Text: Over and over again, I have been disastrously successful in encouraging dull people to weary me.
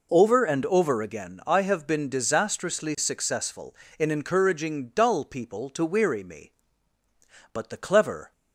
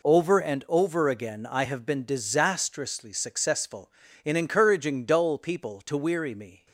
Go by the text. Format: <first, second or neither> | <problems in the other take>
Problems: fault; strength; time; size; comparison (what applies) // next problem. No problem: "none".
second | goes on to say "But the clever"; noticeable; from 7.5 s on; 0.80 s long